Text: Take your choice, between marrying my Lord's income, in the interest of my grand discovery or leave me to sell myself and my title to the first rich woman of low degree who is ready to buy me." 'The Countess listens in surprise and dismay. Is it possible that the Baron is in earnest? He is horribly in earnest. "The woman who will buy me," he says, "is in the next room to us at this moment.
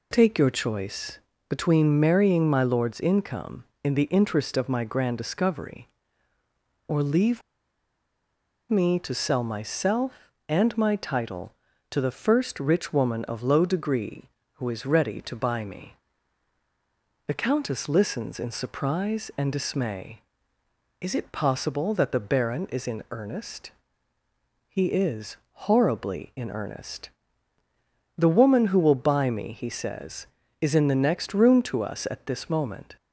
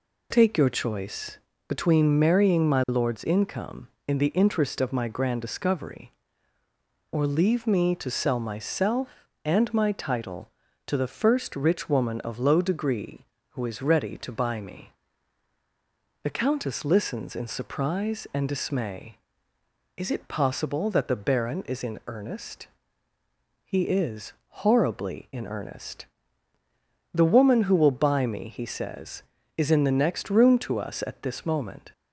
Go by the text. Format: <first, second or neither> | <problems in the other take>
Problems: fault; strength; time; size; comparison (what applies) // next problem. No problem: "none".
second | pauses between "leave" and "me"; strong; at 7.4 s; 1.2 s long